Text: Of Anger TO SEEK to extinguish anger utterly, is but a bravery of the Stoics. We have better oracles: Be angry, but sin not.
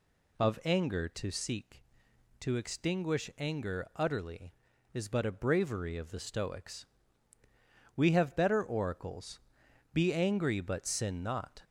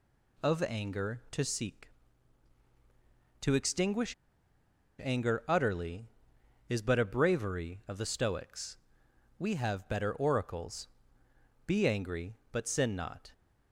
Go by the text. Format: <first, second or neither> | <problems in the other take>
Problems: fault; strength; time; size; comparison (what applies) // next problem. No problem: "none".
first | pauses between "extinguish" and "anger"; noticeable; at 4.1 s; 0.88 s long